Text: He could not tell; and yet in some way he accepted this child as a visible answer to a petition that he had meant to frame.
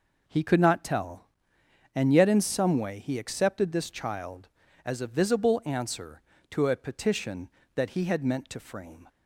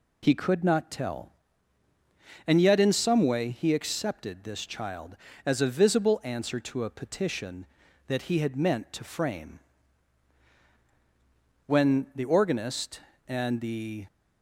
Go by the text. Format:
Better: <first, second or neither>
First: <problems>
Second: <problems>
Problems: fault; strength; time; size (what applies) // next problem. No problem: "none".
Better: first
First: none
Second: goes on to say "When the organist and the"; strong; from 11.6 s on; 2.4 s long